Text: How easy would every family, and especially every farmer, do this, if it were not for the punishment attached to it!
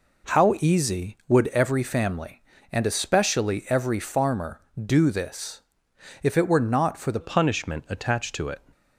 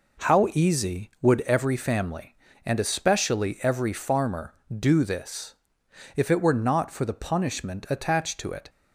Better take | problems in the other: second | changes voice at "punishment"; from 7.2 s on; 1.4 s long

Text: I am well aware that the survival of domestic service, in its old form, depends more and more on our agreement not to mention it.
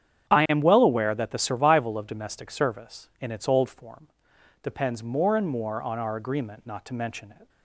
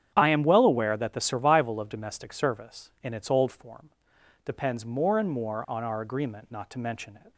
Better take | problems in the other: neither | starts louder than the rest; strong; the same in both

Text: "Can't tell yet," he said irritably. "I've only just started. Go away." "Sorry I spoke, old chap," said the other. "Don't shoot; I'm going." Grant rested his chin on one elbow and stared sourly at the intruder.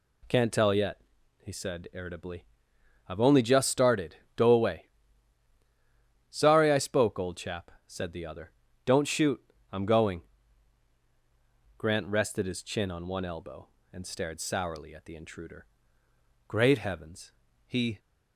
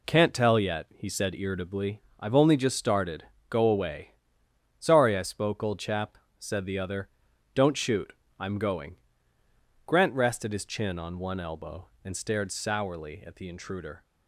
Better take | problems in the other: second | goes on to say "Great heavens he"; from 16.4 s on; 1.5 s long

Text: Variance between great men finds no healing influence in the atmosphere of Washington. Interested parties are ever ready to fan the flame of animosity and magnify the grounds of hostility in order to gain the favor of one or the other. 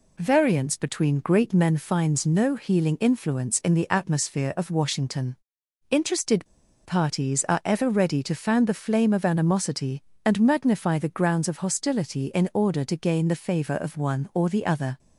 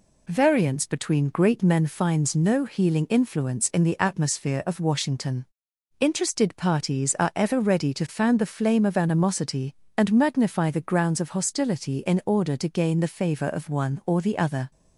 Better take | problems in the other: second | pauses between "Interested" and "parties"; at 6.4 s; 0.39 s long

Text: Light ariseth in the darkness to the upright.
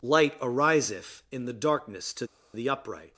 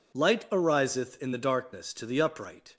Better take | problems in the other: second | pauses between "to" and "the"; slight; at 2.2 s; 0.29 s long

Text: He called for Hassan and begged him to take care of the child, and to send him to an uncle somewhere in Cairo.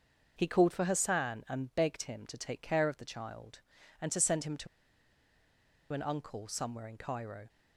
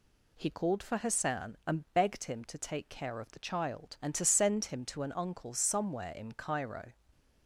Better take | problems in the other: second | starts louder than the rest; until 1.3 s; 6.5 dB // pauses between "to" and "an"; strong; at 4.6 s; 1.2 s long

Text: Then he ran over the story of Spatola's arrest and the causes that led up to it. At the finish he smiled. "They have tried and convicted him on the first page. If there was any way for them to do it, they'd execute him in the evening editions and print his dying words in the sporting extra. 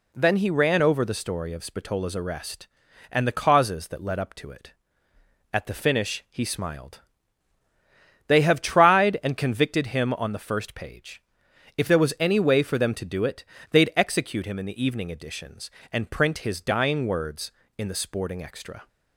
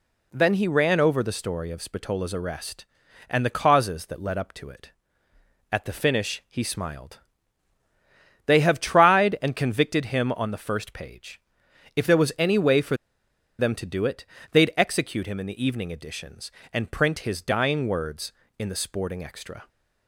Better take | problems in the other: first | pauses between "for" and "them"; noticeable; at 12.9 s; 0.63 s long

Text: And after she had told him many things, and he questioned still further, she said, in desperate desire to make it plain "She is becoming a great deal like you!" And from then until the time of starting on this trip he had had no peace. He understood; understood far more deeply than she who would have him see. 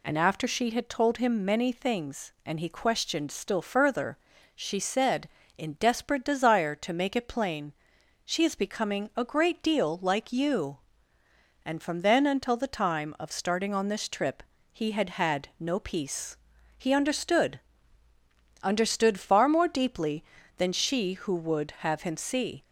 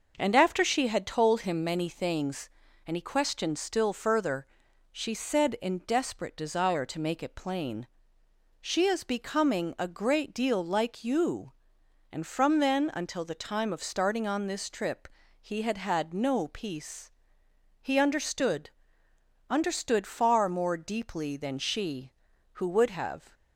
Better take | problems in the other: first | pauses between "plain" and "She"; noticeable; at 7.8 s; 0.76 s long; noticeable in the first // pauses between "trip" and "he"; slight; at 15.0 s; 0.32 s long; slight in the first // stops before "him see"; at 23.3 s

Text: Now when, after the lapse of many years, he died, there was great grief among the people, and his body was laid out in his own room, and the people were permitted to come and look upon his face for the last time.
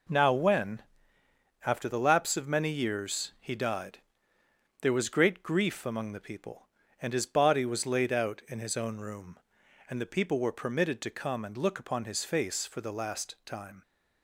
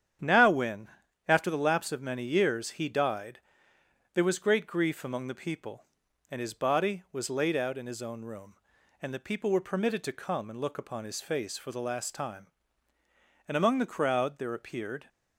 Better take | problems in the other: first | starts louder than the rest; strong; until 1.5 s; 9 dB // goes on to say "And among the crowd there appeared"; from 13.4 s on; 1.6 s long

